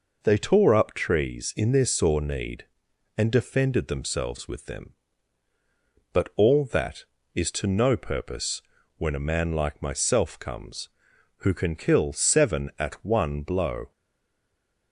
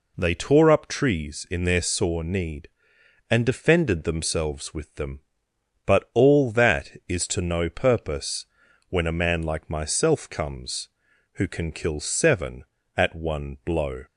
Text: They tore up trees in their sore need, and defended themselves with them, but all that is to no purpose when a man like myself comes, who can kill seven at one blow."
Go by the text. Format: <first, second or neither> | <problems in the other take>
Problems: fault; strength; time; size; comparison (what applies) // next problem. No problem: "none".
second | pauses between "purpose" and "when"; slight; at 8.6 s; 0.36 s long; also in the second // stays silent after the last word; from 13.9 s on; 1.0 s long